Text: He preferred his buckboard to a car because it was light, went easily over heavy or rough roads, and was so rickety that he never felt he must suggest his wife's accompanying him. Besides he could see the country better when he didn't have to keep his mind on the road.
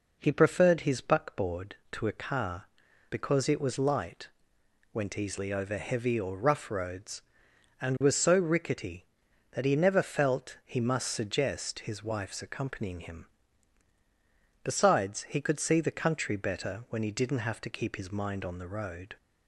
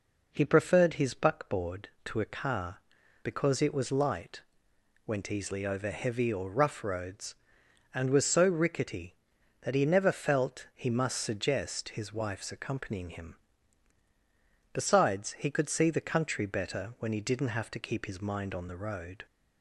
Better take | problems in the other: neither | none

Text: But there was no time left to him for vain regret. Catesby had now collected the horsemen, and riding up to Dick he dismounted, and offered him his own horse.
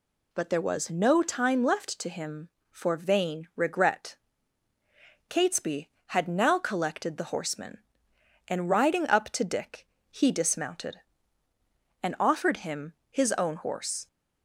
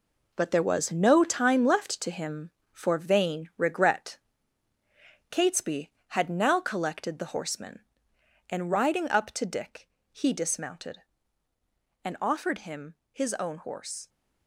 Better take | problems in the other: first | gets quieter; strong; throughout; 9 dB // pauses between "Dick" and "he"; slight; at 9.8 s; 0.22 s long; slight in the first // pauses between "him" and "his"; slight; at 12.9 s; 0.16 s long; slight in the first

